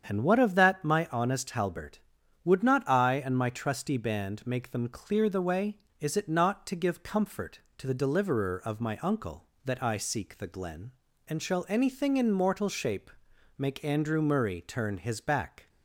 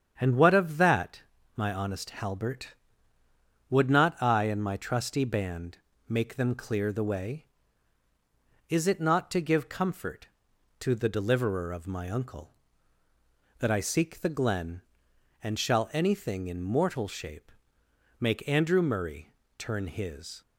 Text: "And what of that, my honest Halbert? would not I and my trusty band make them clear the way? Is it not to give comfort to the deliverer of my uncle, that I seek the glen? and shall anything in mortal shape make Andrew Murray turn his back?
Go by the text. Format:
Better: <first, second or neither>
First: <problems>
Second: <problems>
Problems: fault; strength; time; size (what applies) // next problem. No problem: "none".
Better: first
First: starts louder than the rest; strong; until 1.0 s; 8 dB // pauses between "shape" and "make"; noticeable; at 13.0 s; 0.48 s long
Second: starts louder than the rest; strong; until 1.2 s; 8 dB // pauses between "band" and "make"; slight; at 5.7 s; 0.28 s long // pauses between "shape" and "make"; noticeable; at 17.5 s; 0.68 s long // pauses between "Murray" and "turn"; slight; at 19.3 s; 0.28 s long // stops before "back"; at 20.4 s